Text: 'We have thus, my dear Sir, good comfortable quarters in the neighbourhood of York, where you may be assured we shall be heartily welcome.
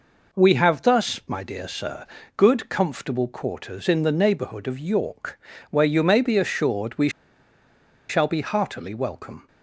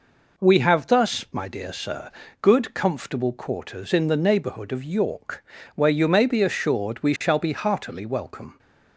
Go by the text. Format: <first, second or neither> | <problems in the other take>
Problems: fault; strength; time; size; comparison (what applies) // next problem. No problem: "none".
second | pauses between "we" and "shall"; at 7.0 s; 0.99 s long